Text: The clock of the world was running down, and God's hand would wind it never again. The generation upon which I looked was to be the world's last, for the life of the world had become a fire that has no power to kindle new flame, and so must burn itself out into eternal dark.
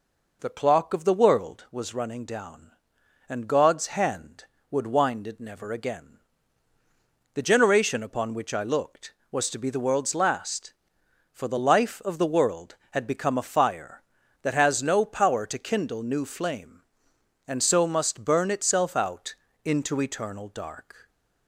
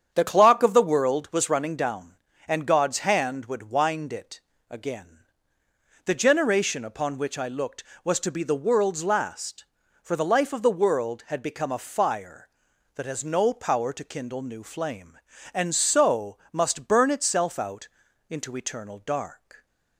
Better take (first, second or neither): first